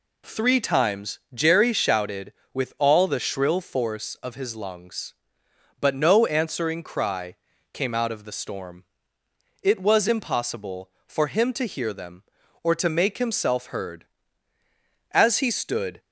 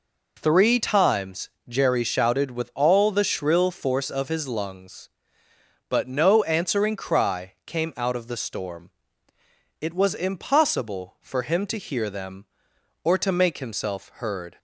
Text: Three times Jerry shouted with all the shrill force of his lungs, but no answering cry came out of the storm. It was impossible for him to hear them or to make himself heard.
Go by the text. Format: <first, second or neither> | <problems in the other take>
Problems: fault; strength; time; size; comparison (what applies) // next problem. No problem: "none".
second | pauses between "times" and "Jerry"; slight; at 1.1 s; 0.16 s long; slight in the second // pauses between "cry" and "came"; slight; at 7.3 s; 0.36 s long // goes on to say "As he stood"; noticeable; from 15.1 s on; 0.88 s long